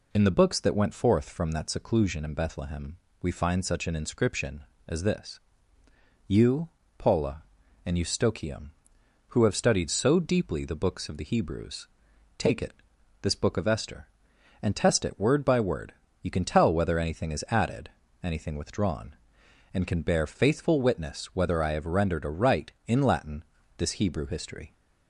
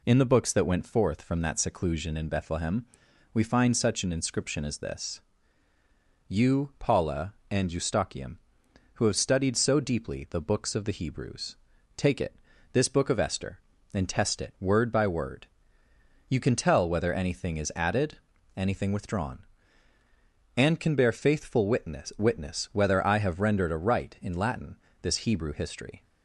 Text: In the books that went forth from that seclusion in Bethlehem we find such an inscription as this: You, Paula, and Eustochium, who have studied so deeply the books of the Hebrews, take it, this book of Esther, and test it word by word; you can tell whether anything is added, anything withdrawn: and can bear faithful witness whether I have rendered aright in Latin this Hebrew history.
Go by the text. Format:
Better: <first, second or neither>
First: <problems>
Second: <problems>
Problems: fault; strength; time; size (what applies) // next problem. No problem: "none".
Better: first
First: pauses between "Bethlehem" and "we"; slight; at 2.9 s; 0.26 s long // pauses between "Latin" and "this"; slight; at 23.4 s; 0.32 s long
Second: pauses between "Bethlehem" and "we"; noticeable; at 2.8 s; 0.46 s long // says "witness" twice; at 22.1 s // pauses between "Latin" and "this"; slight; at 24.7 s; 0.26 s long